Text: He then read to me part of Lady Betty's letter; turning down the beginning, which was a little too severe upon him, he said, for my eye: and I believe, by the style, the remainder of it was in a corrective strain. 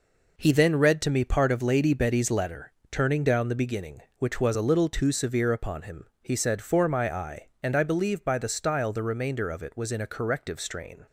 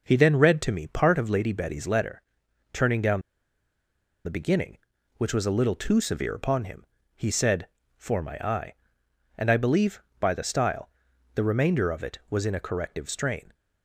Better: first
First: none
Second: pauses between "down" and "the"; at 3.2 s; 1.0 s long

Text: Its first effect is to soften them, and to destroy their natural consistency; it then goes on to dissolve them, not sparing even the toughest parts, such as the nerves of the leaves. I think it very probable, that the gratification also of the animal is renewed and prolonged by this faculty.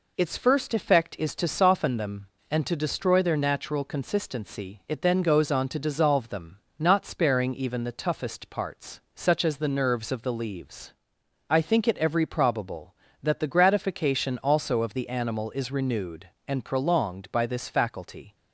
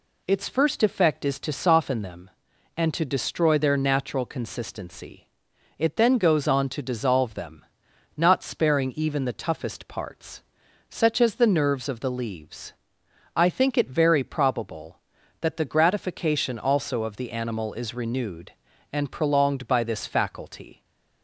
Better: second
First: says "every" for "very"; at 11.9 s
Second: none

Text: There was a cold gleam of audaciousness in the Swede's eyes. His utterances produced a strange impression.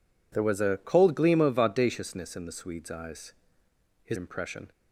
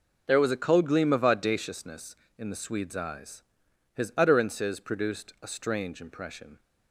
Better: second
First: skips "utterances produced a strange"; at 4.1 s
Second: none

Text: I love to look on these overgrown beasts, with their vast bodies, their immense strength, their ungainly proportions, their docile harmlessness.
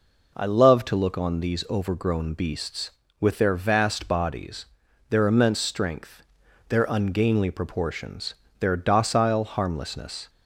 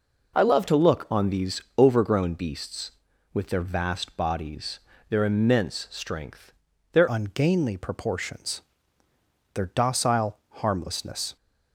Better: first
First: none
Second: pauses between "these" and "overgrown"; slight; at 1.6 s; 0.16 s long // changes voice at "ungainly"; from 7.0 s on; 4.3 s long

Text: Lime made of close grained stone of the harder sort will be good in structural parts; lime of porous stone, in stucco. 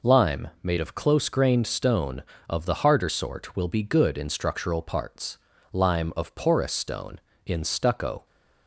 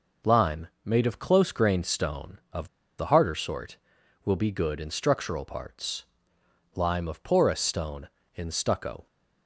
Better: first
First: pauses between "Lime" and "made"; slight; at 0.4 s; 0.16 s long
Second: pauses between "Lime" and "made"; slight; at 0.6 s; 0.16 s long // pauses between "of" and "the"; slight; at 2.6 s; 0.30 s long

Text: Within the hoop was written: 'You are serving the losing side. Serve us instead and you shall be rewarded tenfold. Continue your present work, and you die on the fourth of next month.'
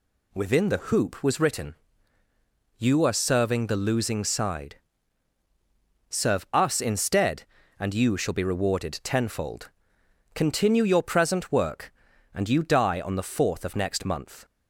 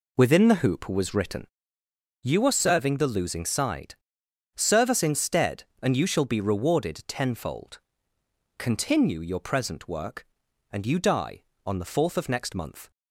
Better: first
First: none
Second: starts louder than the rest; slight; until 1.7 s; 3 dB

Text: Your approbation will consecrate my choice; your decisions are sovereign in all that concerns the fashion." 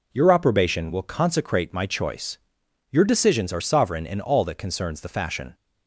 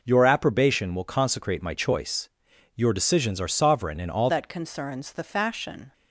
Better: first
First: none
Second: changes voice at "that"; from 4.2 s on; 1.7 s long

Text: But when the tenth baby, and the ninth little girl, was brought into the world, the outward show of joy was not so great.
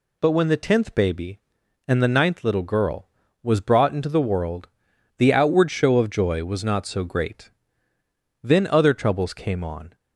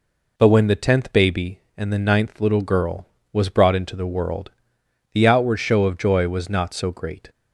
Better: second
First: goes on to say "Then other troubles came on"; from 8.4 s on; 1.5 s long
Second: none

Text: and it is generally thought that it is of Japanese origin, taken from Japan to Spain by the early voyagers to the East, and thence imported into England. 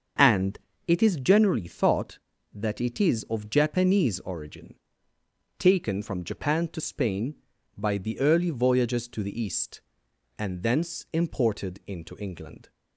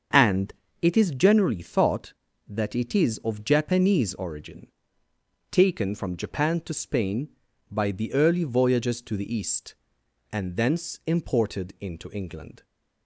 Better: neither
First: starts louder than the rest; until 1.4 s; 6.5 dB // pauses between "and" and "it"; slight; at 0.5 s; 0.30 s long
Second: starts louder than the rest; until 1.4 s; 6.5 dB // pauses between "and" and "it"; slight; at 0.5 s; 0.30 s long

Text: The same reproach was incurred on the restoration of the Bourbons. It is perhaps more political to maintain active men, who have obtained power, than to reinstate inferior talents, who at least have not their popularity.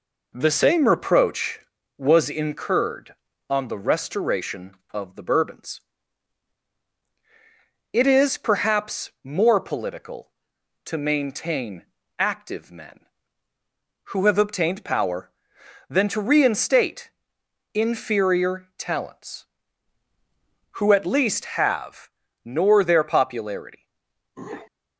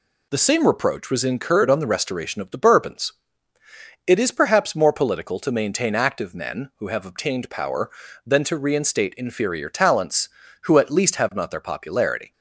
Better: second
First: pauses between "maintain" and "active"; slight; at 11.8 s; 0.32 s long // pauses between "reinstate" and "inferior"; noticeable; at 17.1 s; 0.64 s long // says "nor" for "not"; at 22.4 s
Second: none

